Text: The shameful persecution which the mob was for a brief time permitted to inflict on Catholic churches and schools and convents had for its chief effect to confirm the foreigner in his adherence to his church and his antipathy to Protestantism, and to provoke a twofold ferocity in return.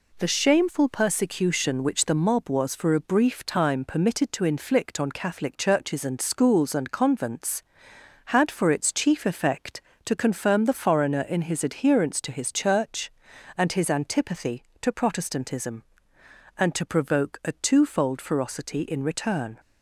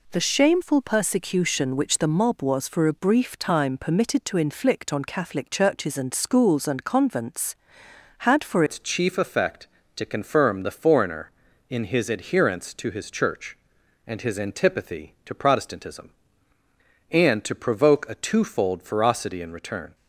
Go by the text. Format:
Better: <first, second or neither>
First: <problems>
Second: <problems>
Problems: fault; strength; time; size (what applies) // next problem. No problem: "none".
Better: first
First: none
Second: changes voice at "its"; from 8.6 s on; 11.3 s long